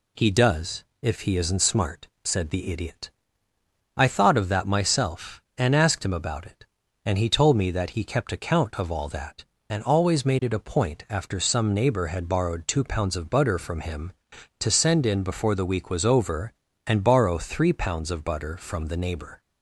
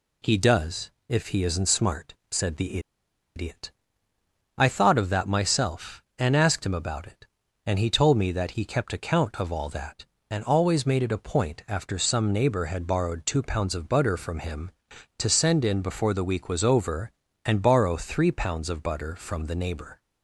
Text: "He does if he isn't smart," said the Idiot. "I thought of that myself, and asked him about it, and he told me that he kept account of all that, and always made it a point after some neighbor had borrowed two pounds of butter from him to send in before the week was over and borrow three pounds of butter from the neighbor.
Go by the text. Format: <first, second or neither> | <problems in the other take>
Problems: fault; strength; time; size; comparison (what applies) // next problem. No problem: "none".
first | pauses between "does" and "if"; slight; at 0.8 s; 0.20 s long; slight in the first // pauses between "the" and "Idiot"; noticeable; at 2.7 s; 0.56 s long